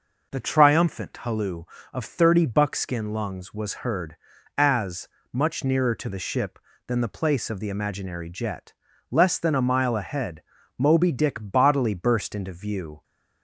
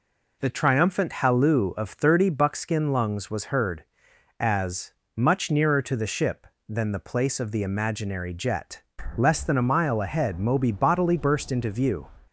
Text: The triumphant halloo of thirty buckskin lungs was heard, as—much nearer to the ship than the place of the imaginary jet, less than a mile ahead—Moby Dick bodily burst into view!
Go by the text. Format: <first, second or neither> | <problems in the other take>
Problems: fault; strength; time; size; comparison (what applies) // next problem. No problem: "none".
first | skips "Dick"; at 10.7 s